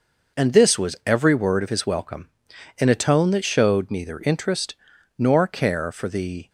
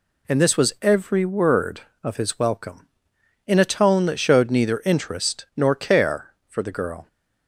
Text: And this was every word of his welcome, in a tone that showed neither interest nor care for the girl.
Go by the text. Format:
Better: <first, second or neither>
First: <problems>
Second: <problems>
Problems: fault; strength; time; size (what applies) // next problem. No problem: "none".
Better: second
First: pauses between "interest" and "nor"; at 4.7 s; 0.44 s long // stops before "girl"; at 6.4 s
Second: none